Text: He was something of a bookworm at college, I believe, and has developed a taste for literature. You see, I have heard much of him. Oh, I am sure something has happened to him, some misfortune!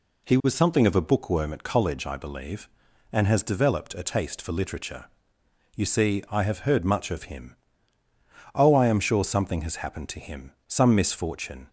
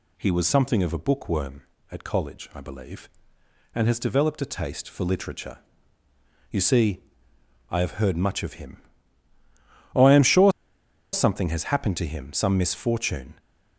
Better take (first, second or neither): first